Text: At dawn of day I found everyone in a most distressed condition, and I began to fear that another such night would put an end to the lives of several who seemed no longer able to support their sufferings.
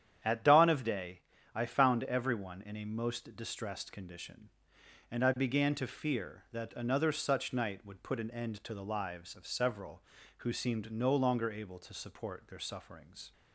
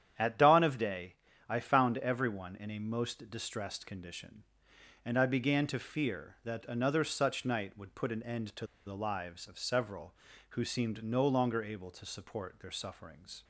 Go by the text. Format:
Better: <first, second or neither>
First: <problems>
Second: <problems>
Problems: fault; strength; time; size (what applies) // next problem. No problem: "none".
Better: first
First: starts louder than the rest; strong; until 1.5 s; 9.5 dB // pauses between "day" and "I"; slight; at 1.2 s; 0.32 s long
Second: starts louder than the rest; strong; until 1.5 s; 9.5 dB // pauses between "day" and "I"; slight; at 1.1 s; 0.32 s long // pauses between "to" and "the"; slight; at 8.6 s; 0.20 s long